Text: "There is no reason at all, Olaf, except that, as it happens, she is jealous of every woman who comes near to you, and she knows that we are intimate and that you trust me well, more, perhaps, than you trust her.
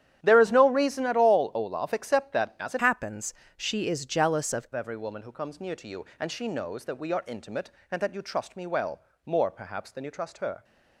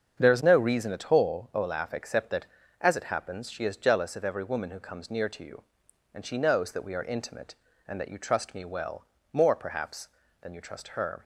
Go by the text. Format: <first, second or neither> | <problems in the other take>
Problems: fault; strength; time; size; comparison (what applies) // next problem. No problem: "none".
second | starts louder than the rest; strong; until 1.2 s; 10.5 dB; strong in the second // changes voice from "happens" to "of"; from 2.8 to 4.6 s; 1.8 s long